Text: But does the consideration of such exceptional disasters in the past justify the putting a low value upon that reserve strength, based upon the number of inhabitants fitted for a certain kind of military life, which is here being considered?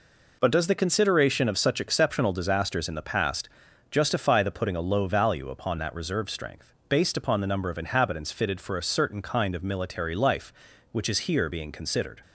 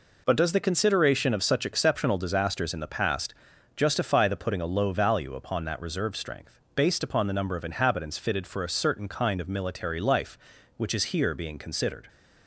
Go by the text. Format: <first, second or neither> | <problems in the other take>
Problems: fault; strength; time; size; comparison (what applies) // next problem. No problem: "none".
neither | pauses between "past" and "justify"; the same in both